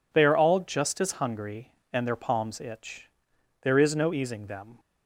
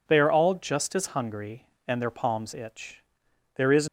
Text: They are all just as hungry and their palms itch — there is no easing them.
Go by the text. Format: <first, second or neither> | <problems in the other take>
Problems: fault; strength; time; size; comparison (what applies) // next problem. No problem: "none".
first | stops before "no easing them"; at 3.8 s